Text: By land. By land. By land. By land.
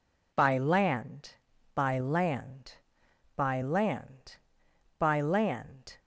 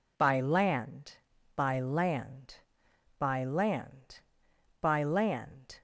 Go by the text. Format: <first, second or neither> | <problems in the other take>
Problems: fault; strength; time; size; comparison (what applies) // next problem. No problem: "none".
neither | none